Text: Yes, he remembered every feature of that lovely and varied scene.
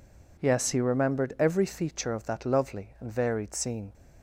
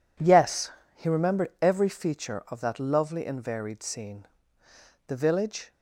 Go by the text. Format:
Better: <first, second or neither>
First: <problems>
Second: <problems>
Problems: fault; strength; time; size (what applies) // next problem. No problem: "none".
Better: first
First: none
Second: goes on to say "The village"; noticeable; from 5.0 s on; 0.64 s long